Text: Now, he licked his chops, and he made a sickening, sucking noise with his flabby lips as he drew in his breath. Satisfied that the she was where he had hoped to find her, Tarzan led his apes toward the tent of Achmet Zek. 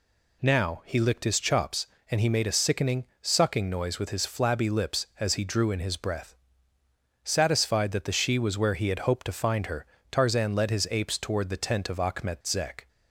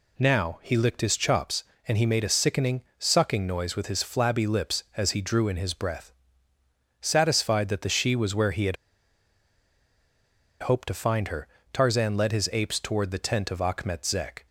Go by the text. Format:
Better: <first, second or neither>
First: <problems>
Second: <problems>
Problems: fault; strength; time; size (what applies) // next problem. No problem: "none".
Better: first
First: none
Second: pauses between "had" and "hoped"; strong; at 8.7 s; 1.8 s long